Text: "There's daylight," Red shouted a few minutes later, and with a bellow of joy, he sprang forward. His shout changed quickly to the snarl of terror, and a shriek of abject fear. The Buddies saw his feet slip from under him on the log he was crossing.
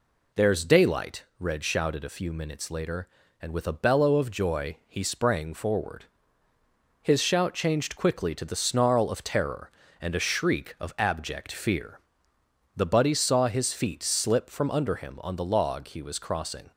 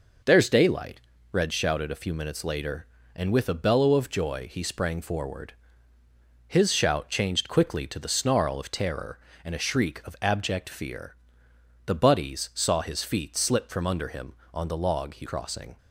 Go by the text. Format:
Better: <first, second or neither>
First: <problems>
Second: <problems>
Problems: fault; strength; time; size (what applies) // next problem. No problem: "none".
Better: first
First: none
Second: skips "was"; at 15.2 s